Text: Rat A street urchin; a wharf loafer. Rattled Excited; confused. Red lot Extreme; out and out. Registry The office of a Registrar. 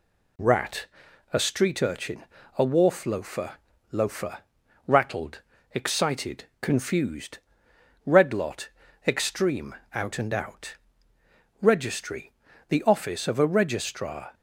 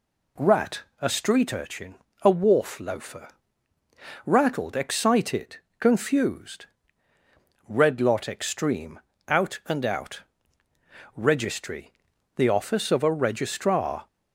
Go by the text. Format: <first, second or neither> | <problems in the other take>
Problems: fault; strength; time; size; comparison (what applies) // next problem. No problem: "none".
second | pauses between "Rat" and "A"; noticeable; at 0.8 s; 0.46 s long; slight in the second // says "loafer" twice; at 3.8 s // pauses between "Rattled" and "Excited"; slight; at 5.3 s; 0.32 s long // pauses between "lot" and "Extreme"; at 8.6 s; 0.40 s long // pauses between "Registry" and "The"; slight; at 12.3 s; 0.34 s long; also in the second